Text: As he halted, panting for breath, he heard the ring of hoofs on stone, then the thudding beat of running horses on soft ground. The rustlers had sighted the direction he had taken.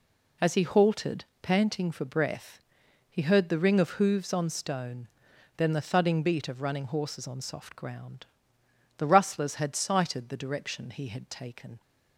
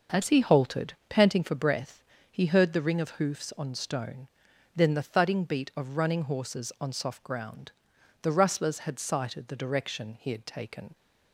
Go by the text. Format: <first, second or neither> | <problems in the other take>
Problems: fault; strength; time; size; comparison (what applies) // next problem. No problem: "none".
neither | none